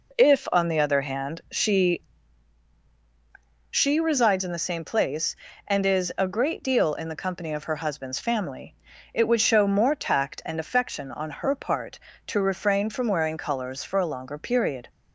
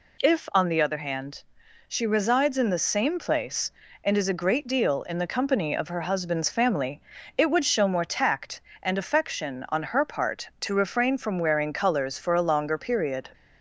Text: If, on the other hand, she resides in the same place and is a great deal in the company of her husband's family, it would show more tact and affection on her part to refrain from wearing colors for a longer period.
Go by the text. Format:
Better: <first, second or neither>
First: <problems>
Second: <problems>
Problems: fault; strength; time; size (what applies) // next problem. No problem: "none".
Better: second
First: says "she" twice; at 3.6 s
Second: none